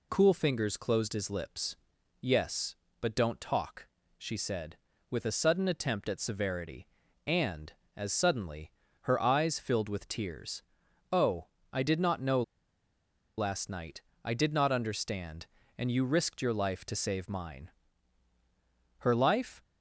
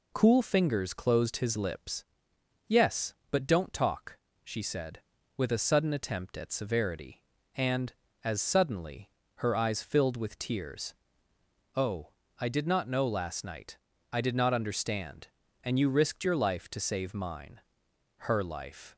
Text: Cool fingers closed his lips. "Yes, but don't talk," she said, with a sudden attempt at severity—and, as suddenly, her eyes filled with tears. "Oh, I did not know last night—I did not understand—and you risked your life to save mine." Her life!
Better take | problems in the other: second | pauses between "know" and "last"; noticeable; at 12.4 s; 0.96 s long

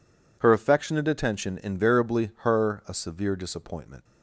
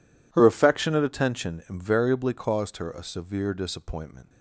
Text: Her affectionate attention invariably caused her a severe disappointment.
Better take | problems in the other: second | skips "caused"; at 2.3 s

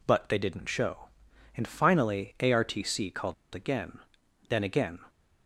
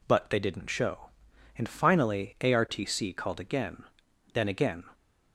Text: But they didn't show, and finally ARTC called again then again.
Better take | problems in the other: second | pauses between "called" and "again"; slight; at 3.3 s; 0.20 s long // pauses between "again" and "then"; noticeable; at 3.9 s; 0.50 s long; noticeable in the second

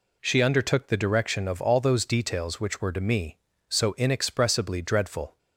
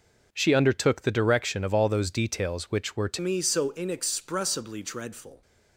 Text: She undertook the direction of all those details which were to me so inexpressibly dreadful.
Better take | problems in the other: first | changes voice at "me"; from 3.1 s on; 2.3 s long

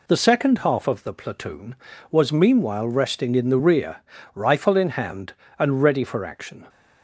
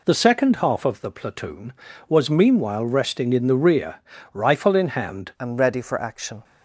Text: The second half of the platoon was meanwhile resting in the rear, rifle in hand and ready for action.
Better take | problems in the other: first | changes voice at "and"; from 5.3 s on; 1.1 s long

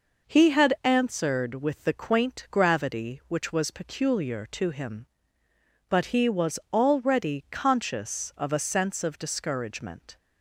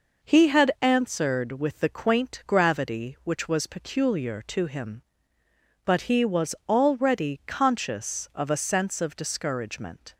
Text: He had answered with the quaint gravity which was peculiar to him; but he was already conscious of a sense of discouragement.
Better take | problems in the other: neither | none

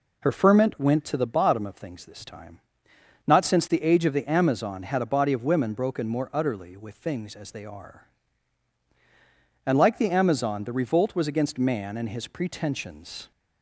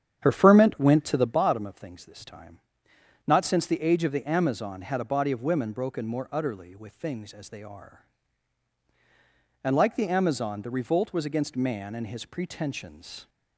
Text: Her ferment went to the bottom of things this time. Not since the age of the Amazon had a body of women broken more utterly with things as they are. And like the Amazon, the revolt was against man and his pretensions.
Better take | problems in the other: first | starts louder than the rest; strong; until 1.5 s; 8.5 dB

